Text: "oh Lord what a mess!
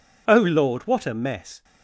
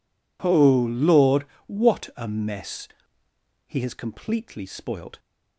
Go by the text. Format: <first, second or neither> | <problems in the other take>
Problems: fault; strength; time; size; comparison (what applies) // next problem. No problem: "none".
first | pauses between "Lord" and "what"; slight; at 1.4 s; 0.22 s long // goes on to say "He has completely spoilt"; from 3.6 s on; 1.5 s long